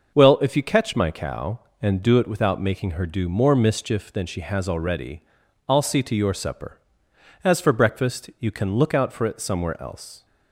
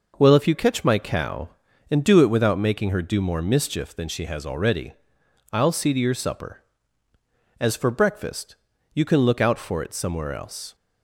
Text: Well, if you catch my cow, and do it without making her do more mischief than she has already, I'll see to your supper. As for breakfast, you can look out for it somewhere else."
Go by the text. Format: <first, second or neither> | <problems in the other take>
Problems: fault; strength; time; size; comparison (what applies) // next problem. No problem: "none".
neither | none